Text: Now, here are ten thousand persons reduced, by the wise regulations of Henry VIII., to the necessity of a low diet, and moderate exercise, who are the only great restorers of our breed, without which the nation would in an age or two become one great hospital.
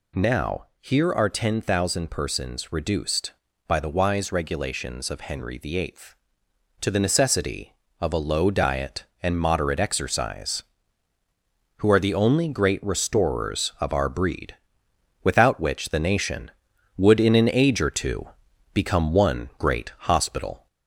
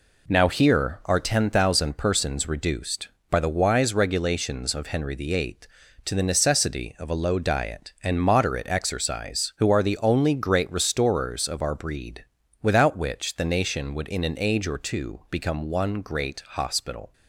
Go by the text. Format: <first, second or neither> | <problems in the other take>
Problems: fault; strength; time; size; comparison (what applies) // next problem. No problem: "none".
second | gets louder; slight; throughout; 2.5 dB // pauses between "two" and "become"; at 18.2 s; 0.44 s long